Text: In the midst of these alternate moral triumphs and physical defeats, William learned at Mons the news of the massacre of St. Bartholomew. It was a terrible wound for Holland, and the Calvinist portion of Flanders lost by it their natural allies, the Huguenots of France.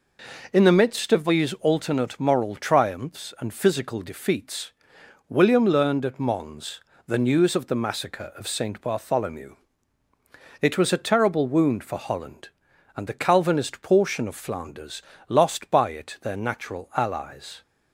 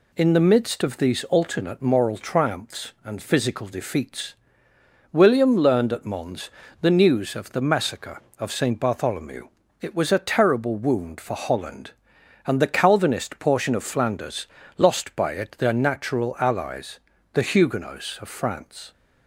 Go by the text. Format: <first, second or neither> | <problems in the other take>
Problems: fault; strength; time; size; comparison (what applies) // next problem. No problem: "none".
second | pauses between "Mons" and "the"; slight; at 6.8 s; 0.26 s long; slight in the second // pauses between "Flanders" and "lost"; slight; at 15.0 s; 0.26 s long; slight in the second // stops before "the Huguenots of France"; at 17.6 s